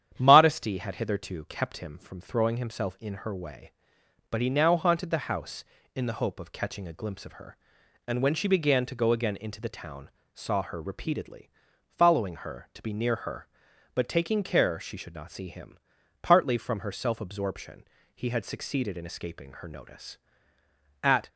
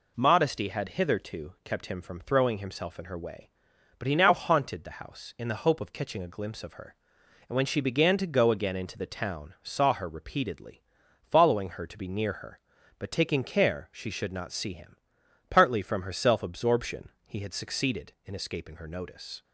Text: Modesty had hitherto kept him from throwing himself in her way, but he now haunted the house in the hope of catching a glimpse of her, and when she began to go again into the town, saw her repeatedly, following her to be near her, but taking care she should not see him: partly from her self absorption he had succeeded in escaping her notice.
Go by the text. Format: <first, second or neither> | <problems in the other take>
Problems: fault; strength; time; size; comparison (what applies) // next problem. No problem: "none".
second | starts louder than the rest; strong; until 1.1 s; 9.5 dB // pauses between "absorption" and "he"; slight; at 17.8 s; 0.32 s long; slight in the second // goes on to say "At"; slight; from 21.0 s on; 0.28 s long